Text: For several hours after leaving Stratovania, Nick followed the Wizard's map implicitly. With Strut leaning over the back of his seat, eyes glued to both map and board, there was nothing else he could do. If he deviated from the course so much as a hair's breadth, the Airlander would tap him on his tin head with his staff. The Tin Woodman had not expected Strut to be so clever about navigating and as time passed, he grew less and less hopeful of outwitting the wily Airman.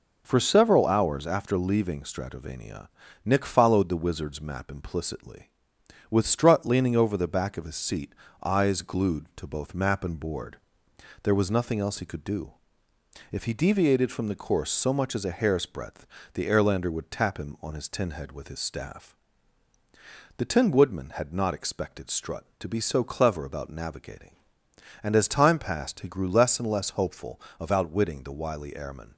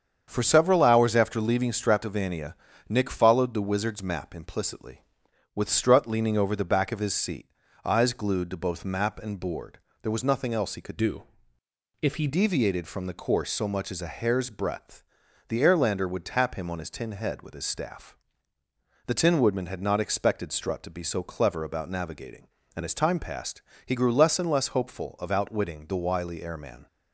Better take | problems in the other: first | starts louder than the rest; strong; until 1.2 s; 7.5 dB // changes voice from "do" to "he"; from 10.9 to 12.2 s; 1.3 s long

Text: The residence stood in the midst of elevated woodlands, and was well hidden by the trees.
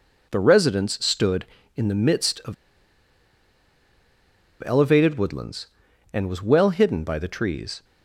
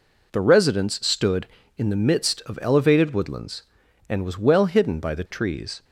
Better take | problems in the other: second | pauses between "of" and "elevated"; strong; at 2.5 s; 2.1 s long

